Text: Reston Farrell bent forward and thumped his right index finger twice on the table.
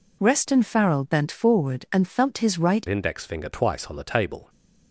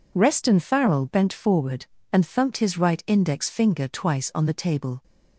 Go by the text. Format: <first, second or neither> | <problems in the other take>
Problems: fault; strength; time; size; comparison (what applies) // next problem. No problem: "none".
second | changes voice at "index"; from 2.8 s on; 1.6 s long